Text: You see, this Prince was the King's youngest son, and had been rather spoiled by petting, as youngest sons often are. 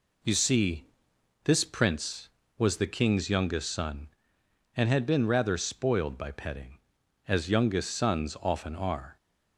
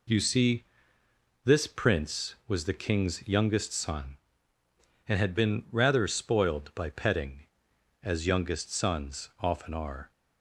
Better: neither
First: none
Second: none

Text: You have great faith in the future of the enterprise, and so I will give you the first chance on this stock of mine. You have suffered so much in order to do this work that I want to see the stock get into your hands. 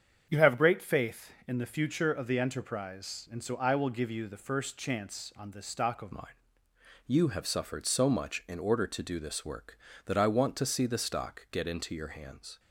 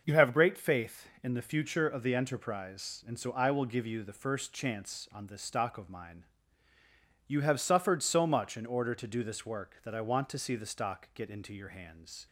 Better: second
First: starts louder than the rest; strong; until 1.2 s; 7.5 dB // changes voice at "mine"; from 6.1 s on; 6.4 s long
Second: starts louder than the rest; until 1.0 s; 6 dB

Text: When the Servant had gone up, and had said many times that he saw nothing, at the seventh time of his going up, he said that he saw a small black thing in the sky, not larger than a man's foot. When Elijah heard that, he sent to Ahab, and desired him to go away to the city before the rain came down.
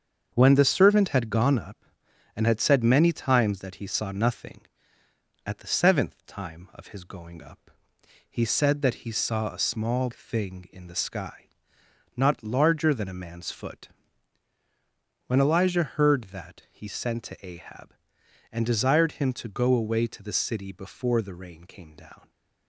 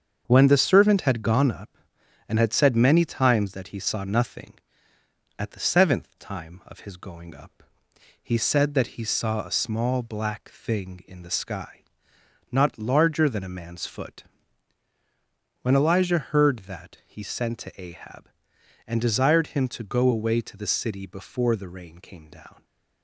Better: second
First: starts louder than the rest; until 1.3 s; 7 dB // skips "black"; at 10.1 s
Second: starts louder than the rest; until 1.2 s; 7 dB

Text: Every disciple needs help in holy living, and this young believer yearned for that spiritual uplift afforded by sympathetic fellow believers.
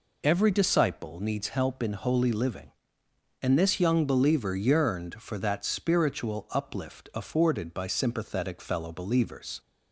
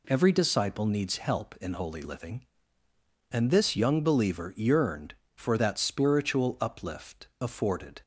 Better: first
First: none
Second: stops before "by sympathetic fellow believers"; at 8.0 s

